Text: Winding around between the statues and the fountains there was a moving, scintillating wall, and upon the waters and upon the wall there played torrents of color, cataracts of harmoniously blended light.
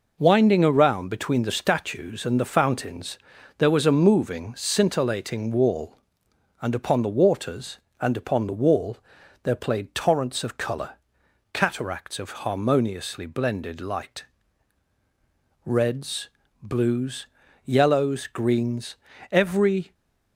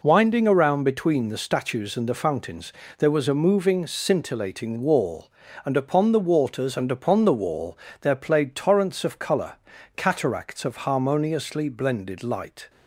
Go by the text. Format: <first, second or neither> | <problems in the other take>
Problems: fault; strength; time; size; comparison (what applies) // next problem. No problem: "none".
second | pauses between "fountains" and "there"; at 3.1 s; 0.40 s long; slight in the second // pauses between "wall" and "there"; at 8.9 s; 0.44 s long; slight in the second // goes on to say "Reds blues yellows greens every"; strong; from 15.6 s on; 4.2 s long